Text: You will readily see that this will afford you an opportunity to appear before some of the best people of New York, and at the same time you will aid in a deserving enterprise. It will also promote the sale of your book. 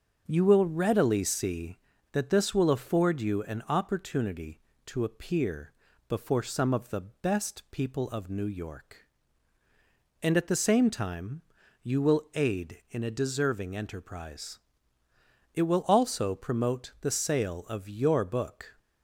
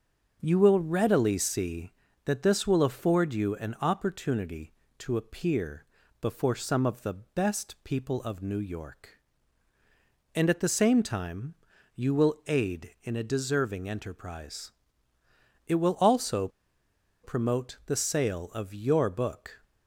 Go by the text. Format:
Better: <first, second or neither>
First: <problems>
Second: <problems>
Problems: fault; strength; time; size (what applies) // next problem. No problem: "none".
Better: first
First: starts louder than the rest; until 1.2 s; 7 dB // pauses between "appear" and "before"; slight; at 5.7 s; 0.36 s long // pauses between "time" and "you"; at 11.4 s; 0.40 s long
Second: starts louder than the rest; until 1.4 s; 7 dB // pauses between "appear" and "before"; slight; at 5.8 s; 0.36 s long // pauses between "time" and "you"; at 11.5 s; 0.40 s long // pauses between "also" and "promote"; noticeable; at 16.4 s; 0.75 s long